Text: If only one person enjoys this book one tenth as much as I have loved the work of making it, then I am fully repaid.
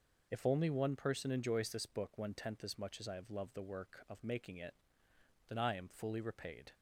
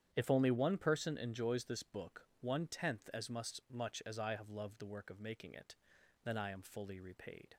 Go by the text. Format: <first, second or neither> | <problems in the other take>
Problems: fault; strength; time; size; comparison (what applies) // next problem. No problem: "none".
first | starts louder than the rest; strong; until 1.1 s; 9.5 dB // pauses between "book" and "one"; slight; at 2.2 s; 0.16 s long // says "much" twice; at 3.7 s